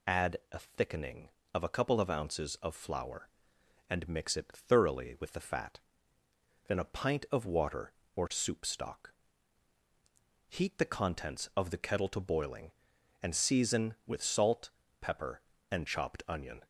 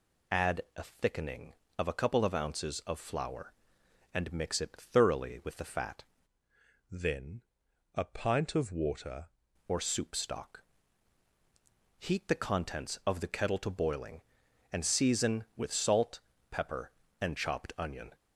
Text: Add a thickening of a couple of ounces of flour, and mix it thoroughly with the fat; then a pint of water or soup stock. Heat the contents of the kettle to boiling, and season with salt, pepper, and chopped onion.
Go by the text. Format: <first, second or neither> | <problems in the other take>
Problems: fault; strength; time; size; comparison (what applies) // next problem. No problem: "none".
first | changes voice from "then" to "water"; from 6.8 to 9.2 s; 2.4 s long // pauses between "then" and "a"; noticeable; at 7.4 s; 0.50 s long